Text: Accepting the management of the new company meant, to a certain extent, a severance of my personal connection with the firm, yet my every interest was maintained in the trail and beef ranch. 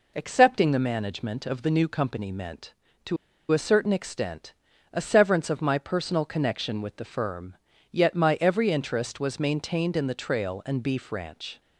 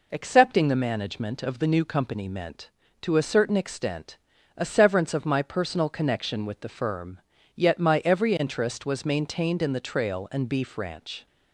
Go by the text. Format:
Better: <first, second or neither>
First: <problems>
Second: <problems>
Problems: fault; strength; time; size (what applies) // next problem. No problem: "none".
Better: second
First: pauses between "to" and "a"; slight; at 3.1 s; 0.35 s long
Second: none